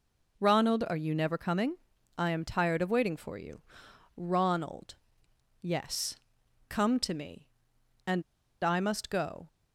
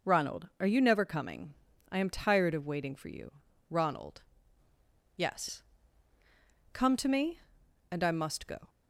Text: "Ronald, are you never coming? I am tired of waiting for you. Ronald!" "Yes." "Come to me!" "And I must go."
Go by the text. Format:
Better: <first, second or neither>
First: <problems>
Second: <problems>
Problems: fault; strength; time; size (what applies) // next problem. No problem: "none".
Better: second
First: pauses between "And" and "I"; at 8.2 s; 0.38 s long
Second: none